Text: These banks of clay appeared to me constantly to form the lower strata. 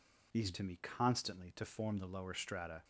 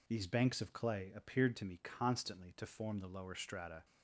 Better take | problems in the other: second | skips "banks of clay appeared"; at 0.5 s

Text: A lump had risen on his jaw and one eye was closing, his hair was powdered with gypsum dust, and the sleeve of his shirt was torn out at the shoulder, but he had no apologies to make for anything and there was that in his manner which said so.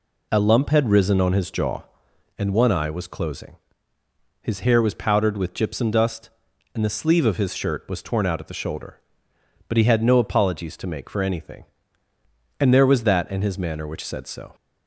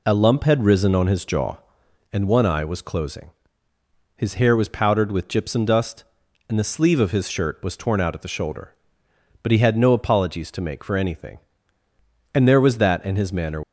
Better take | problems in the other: first | stops before "which said so"; at 13.6 s

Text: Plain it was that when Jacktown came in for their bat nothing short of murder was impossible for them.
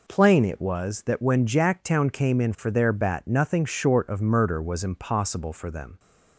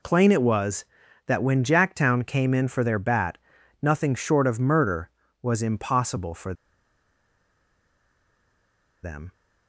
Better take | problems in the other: first | pauses between "bat" and "nothing"; at 3.3 s; 0.44 s long // pauses between "for" and "them"; strong; at 6.5 s; 2.5 s long

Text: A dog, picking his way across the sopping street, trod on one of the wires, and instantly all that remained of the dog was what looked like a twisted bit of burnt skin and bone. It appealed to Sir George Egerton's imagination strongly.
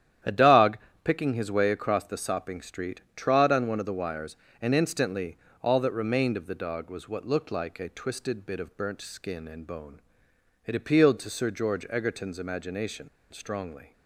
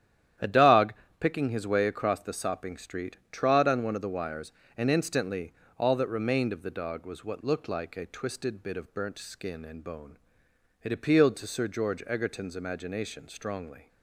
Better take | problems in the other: second | starts louder than the rest; strong; until 1.5 s; 10.5 dB; strong in the second // pauses between "instantly" and "all"; slight; at 5.3 s; 0.26 s long; slight in the second // pauses between "imagination" and "strongly"; slight; at 13.0 s; 0.23 s long

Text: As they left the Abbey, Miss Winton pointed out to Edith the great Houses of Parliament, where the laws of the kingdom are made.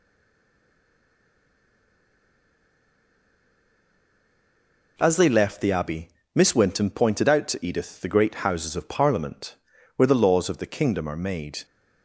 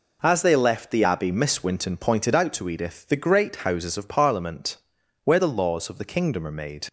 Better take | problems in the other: second | stays silent before the first word; strong; until 4.9 s; 4.9 s long

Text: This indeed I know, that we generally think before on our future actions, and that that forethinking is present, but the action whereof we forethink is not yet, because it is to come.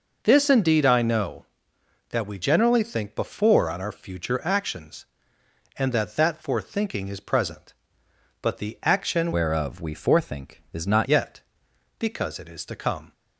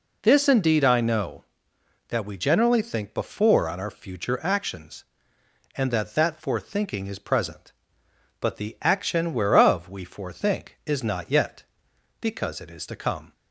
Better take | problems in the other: second | changes voice from "whereof" to "not"; from 9.3 to 11.0 s; 1.7 s long

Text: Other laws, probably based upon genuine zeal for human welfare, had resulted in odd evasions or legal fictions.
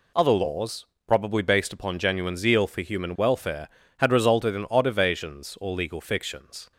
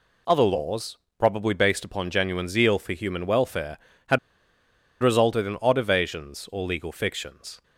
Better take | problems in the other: first | pauses between "had" and "resulted"; noticeable; at 4.1 s; 0.83 s long

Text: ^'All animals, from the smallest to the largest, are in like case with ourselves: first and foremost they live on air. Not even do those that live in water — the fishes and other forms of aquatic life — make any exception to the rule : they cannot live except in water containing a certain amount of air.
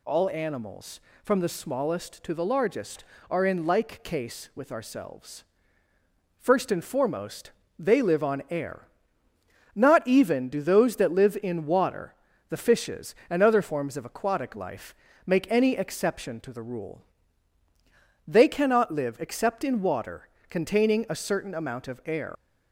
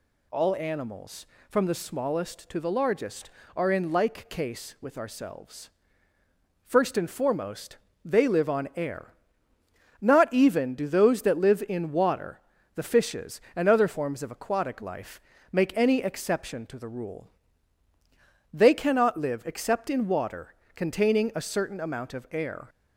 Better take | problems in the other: second | pauses between "foremost" and "they"; slight; at 7.5 s; 0.28 s long; slight in the second // pauses between "water" and "containing"; slight; at 20.2 s; 0.22 s long; slight in the second // leaves "air" unfinished; at 22.3 s; 75 ms

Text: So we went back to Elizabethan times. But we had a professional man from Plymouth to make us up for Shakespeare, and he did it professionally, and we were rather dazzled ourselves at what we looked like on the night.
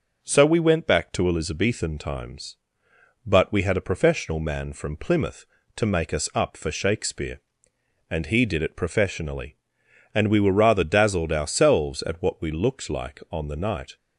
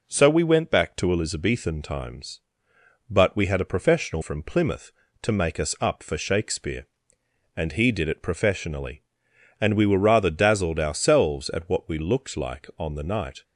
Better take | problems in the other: first | skips "man"; at 4.2 s

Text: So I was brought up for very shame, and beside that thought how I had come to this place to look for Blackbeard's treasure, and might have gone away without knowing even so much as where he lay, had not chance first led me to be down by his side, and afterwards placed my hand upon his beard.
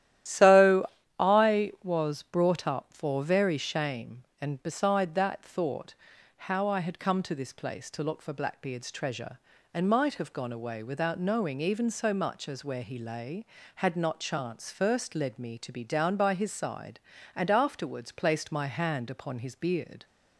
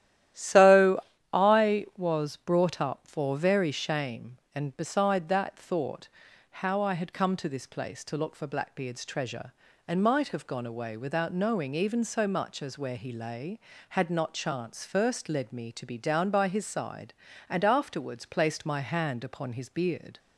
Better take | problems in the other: second | loses the start of "So"; at 0.2 s; 35 ms // starts louder than the rest; strong; until 1.5 s; 12.5 dB; strong in the second // pauses between "So" and "I"; slight; at 0.8 s; 0.32 s long; slight in the second // pauses between "thought" and "how"; at 5.9 s; 0.42 s long; also in the second

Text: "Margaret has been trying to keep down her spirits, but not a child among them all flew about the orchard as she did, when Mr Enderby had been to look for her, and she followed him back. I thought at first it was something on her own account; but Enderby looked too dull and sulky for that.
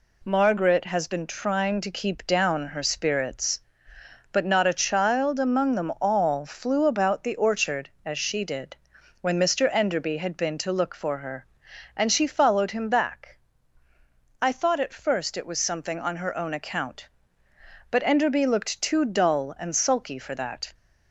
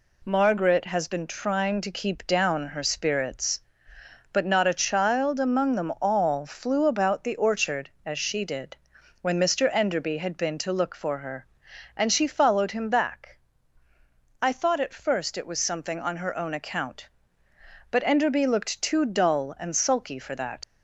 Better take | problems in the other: first | leaves "that" unfinished; at 20.6 s; 105 ms

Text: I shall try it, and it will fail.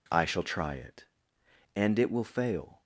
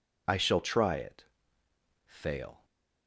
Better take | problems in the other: first | skips "and it will"; at 1.6 s

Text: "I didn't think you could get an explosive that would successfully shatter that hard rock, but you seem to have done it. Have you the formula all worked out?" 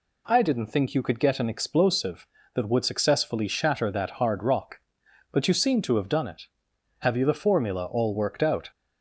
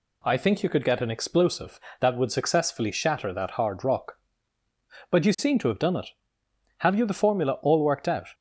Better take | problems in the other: first | skips "didn't"; at 0.3 s

